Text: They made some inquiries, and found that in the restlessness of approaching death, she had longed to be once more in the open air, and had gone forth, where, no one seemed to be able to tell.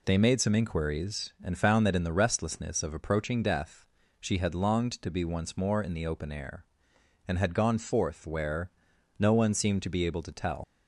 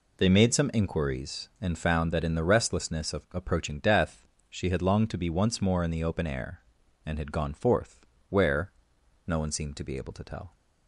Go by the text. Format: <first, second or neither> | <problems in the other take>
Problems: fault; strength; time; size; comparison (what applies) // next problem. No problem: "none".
second | leaves "tell" unfinished; at 10.6 s; 70 ms